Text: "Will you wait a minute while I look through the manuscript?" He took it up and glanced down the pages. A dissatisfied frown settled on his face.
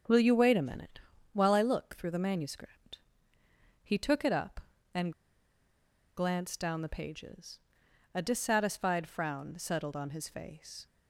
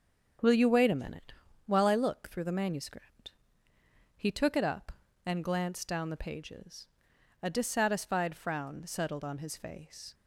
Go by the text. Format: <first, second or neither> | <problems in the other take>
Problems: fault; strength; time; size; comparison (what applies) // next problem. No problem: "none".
second | starts louder than the rest; noticeable; until 1.4 s; 6 dB; also in the second // pauses between "minute" and "while"; slight; at 1.0 s; 0.32 s long; slight in the second // pauses between "and" and "glanced"; at 5.1 s; 1.0 s long